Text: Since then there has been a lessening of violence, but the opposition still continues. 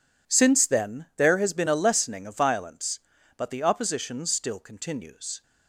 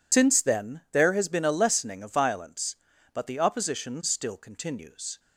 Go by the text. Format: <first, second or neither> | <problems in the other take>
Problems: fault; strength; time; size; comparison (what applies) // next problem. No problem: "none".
first | loses the start of "Since"; at 0.1 s; 100 ms